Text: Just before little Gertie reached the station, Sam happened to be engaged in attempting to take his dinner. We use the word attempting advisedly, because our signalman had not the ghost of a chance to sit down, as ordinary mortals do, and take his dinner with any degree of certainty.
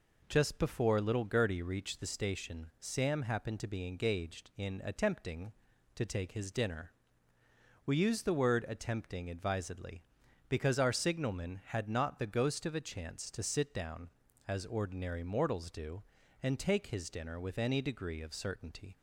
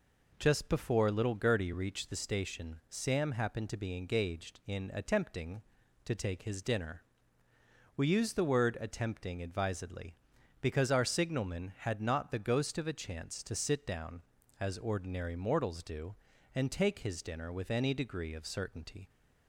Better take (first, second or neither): neither